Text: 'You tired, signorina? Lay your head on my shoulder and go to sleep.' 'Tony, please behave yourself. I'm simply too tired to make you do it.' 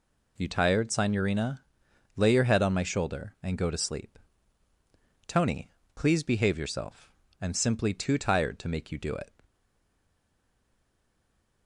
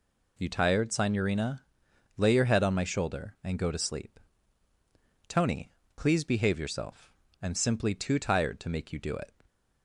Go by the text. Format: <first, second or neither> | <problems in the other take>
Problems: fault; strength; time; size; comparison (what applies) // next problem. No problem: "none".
second | stays silent after the last word; from 9.4 s on; 2.2 s long